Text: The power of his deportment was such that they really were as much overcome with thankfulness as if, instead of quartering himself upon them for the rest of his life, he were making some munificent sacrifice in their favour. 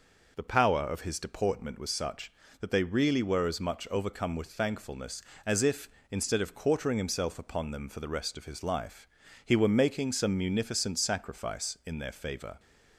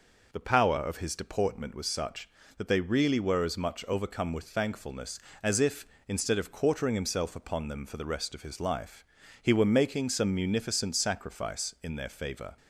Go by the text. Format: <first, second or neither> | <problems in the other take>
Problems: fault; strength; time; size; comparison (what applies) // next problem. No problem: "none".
neither | none